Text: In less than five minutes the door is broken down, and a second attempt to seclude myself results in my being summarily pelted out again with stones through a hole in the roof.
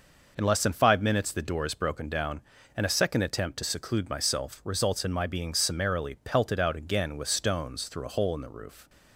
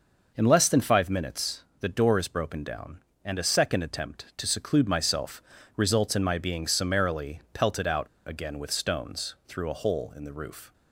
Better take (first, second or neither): first